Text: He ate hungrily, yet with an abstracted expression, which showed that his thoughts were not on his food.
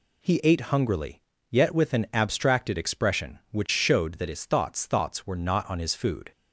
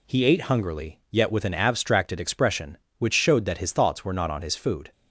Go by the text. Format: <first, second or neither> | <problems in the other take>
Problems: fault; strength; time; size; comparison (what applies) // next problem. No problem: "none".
second | says "thoughts" twice; at 4.8 s